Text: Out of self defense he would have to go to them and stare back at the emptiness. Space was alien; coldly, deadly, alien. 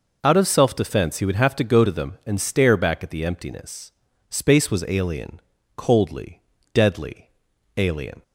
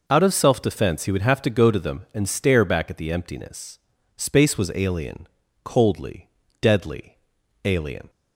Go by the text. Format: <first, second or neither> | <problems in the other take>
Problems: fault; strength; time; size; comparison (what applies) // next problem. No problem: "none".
neither | none